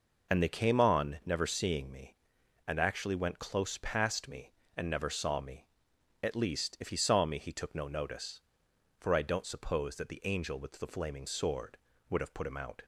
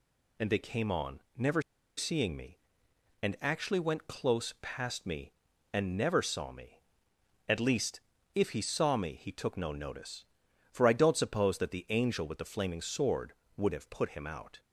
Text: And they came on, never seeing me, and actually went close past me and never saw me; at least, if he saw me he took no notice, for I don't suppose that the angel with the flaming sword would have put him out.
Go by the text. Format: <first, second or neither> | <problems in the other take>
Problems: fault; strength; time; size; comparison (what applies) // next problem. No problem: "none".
first | pauses between "never" and "seeing"; at 1.6 s; 0.36 s long